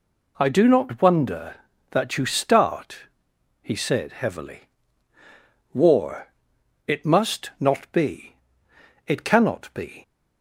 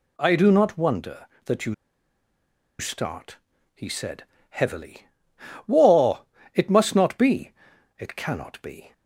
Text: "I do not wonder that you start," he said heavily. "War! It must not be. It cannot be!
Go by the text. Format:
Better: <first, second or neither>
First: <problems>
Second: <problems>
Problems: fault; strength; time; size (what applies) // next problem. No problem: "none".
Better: first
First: none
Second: pauses between "you" and "start"; at 1.7 s; 1.0 s long // pauses between "said" and "heavily"; slight; at 4.2 s; 0.26 s long